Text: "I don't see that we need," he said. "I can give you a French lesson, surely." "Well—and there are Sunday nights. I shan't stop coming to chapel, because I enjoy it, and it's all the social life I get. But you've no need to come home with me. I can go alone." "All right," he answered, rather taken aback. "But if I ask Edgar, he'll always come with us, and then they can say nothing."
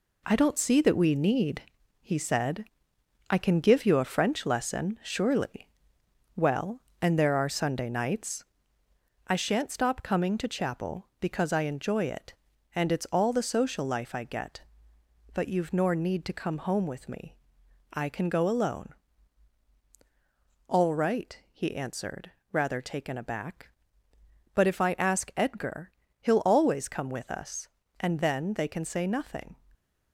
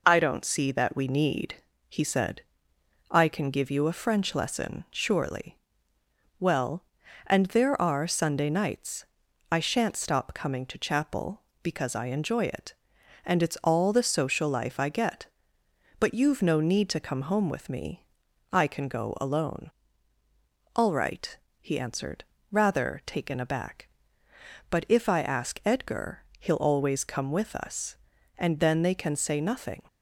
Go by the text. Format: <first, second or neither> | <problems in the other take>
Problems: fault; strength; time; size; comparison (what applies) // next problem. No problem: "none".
second | says "nor" for "no"; at 15.7 s